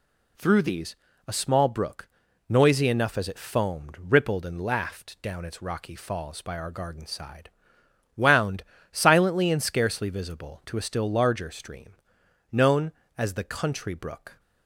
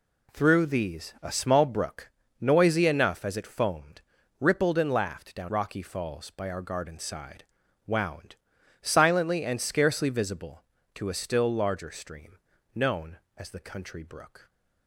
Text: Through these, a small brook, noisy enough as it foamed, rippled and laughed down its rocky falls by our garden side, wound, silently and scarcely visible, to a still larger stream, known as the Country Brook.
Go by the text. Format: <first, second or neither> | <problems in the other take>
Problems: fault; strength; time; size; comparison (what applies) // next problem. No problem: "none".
first | skips "its"; at 5.4 s